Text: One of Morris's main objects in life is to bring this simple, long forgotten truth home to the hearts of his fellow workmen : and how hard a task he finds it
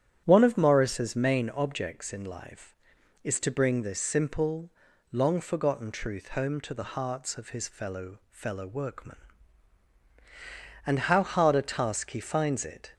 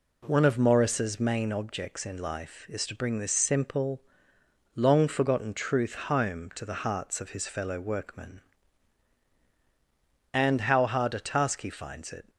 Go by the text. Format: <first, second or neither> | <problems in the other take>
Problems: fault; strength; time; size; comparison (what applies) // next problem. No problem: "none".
second | starts louder than the rest; strong; until 1.2 s; 10 dB // says "fellow" twice; at 8.2 s